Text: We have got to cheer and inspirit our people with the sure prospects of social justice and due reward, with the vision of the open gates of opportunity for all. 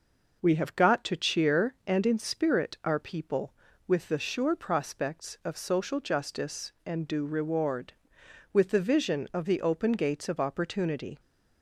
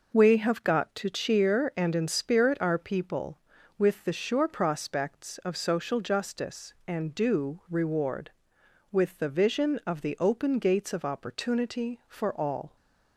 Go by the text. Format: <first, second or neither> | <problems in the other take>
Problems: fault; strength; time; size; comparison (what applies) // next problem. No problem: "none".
second | stops before "for all"; at 11.1 s